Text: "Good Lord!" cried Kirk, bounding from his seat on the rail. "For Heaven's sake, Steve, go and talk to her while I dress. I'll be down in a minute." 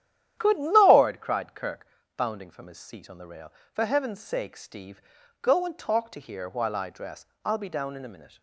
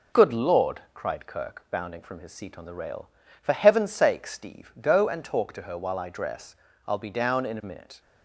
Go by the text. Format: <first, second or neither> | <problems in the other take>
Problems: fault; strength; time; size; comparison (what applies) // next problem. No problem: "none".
second | starts louder than the rest; strong; until 1.4 s; 10.5 dB // says "here" for "her"; at 6.1 s